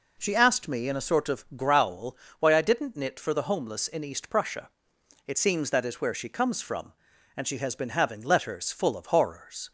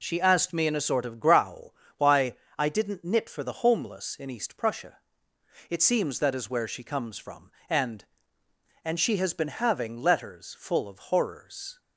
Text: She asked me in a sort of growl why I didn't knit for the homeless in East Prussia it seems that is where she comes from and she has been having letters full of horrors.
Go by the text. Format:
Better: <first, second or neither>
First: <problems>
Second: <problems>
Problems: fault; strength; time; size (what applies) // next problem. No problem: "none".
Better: first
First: pauses between "growl" and "why"; slight; at 2.1 s; 0.24 s long // pauses between "Prussia" and "it"; noticeable; at 4.6 s; 0.58 s long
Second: pauses between "growl" and "why"; slight; at 1.7 s; 0.20 s long // pauses between "why" and "I"; slight; at 2.3 s; 0.22 s long // pauses between "Prussia" and "it"; noticeable; at 4.9 s; 0.72 s long // says "and" twice; at 8.8 s // pauses between "of" and "horrors"; slight; at 10.9 s; 0.16 s long